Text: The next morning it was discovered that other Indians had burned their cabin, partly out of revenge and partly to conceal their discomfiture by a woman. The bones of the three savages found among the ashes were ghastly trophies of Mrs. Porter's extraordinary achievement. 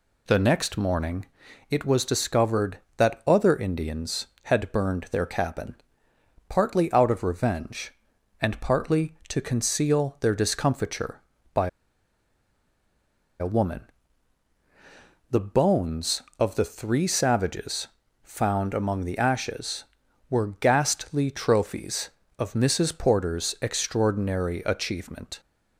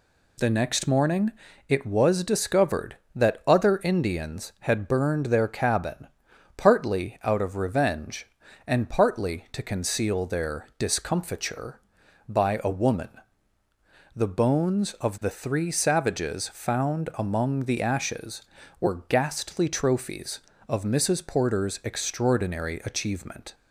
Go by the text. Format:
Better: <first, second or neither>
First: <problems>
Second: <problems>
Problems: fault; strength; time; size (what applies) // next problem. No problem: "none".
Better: second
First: pauses between "morning" and "it"; at 1.2 s; 0.44 s long // pauses between "by" and "a"; strong; at 11.6 s; 1.7 s long // pauses between "savages" and "found"; slight; at 17.8 s; 0.34 s long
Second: pauses between "morning" and "it"; slight; at 1.3 s; 0.34 s long